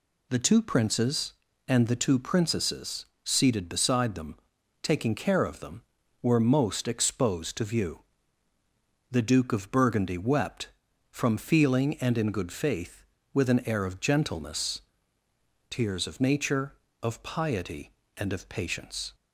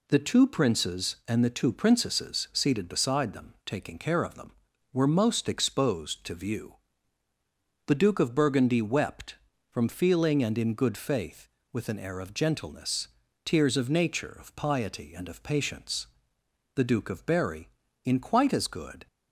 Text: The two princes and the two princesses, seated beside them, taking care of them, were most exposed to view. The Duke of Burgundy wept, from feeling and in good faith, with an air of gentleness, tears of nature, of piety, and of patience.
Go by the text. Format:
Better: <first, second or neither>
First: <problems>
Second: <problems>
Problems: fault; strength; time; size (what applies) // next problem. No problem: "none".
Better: first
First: none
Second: goes on to say "The Duke of Berry in quite as good"; strong; from 16.7 s on; 2.3 s long